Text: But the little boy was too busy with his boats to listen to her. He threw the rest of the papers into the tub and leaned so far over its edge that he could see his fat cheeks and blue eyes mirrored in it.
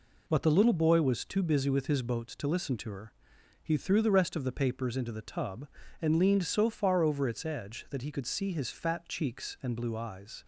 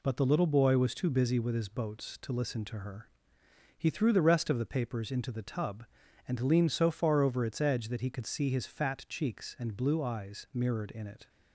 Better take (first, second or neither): second